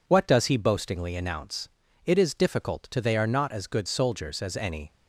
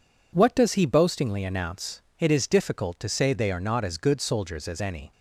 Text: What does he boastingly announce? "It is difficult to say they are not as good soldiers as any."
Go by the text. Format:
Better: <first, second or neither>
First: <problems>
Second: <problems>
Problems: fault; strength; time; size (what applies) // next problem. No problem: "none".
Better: second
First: skips "say"; at 2.9 s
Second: none